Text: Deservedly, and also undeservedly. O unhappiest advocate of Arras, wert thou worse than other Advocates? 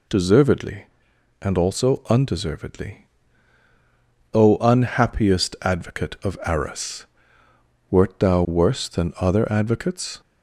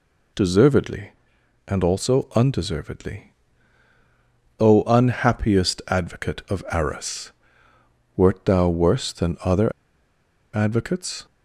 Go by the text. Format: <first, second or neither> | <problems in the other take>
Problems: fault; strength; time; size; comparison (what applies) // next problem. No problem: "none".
first | pauses between "other" and "Advocates"; noticeable; at 9.7 s; 0.83 s long